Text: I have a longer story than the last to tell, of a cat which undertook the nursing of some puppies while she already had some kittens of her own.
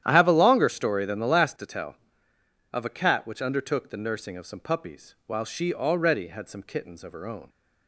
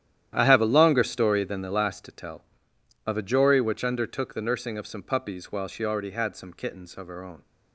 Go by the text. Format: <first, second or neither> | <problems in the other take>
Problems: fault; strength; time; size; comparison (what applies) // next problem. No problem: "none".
first | starts louder than the rest; strong; until 1.3 s; 11 dB; strong in the first // says "jory" for "cat"; at 3.2 s